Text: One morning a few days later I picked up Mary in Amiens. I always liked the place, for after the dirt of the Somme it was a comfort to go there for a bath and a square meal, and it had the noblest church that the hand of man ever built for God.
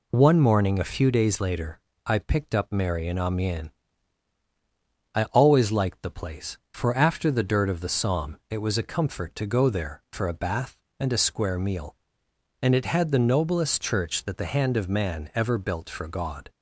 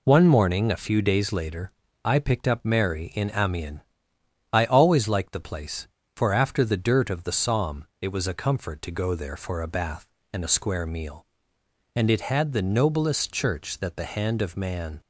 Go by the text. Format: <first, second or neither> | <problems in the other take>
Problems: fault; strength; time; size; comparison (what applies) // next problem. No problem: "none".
first | pauses between "later" and "I"; slight; at 1.7 s; 0.34 s long; slight in the first // pauses between "Somme" and "it"; slight; at 7.8 s; 0.16 s long // stops before "ever built for God"; at 15.0 s